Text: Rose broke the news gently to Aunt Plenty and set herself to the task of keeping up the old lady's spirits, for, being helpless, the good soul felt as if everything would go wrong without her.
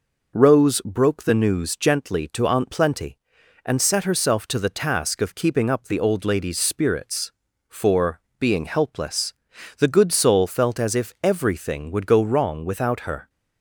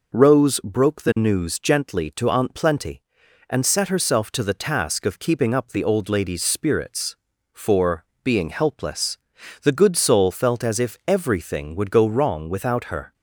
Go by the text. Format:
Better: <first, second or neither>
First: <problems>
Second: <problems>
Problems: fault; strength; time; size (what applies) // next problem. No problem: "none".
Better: neither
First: none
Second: none